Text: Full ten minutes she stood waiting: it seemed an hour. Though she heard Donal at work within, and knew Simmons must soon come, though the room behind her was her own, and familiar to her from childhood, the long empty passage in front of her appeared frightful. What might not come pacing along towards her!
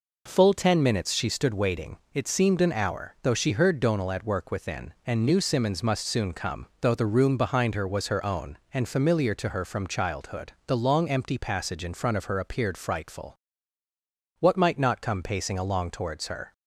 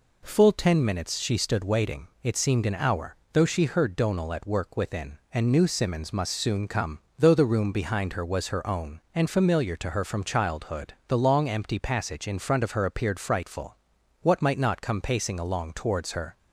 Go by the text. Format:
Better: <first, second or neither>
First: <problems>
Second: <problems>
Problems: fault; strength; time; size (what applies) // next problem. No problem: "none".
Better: neither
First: none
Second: none